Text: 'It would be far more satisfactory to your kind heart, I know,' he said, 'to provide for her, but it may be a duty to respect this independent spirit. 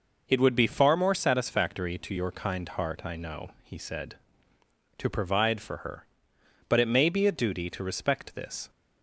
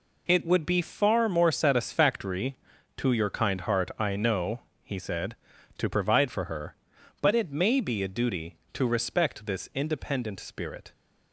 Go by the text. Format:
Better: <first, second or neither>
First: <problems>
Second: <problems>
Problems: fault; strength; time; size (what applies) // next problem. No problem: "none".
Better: second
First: stops before "independent spirit"; at 8.6 s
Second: none